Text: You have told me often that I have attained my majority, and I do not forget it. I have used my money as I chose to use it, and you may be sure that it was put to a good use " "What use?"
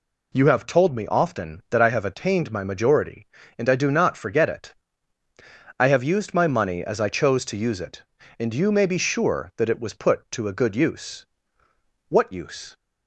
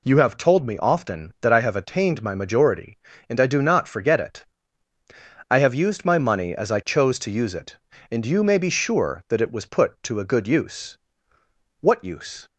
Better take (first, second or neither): neither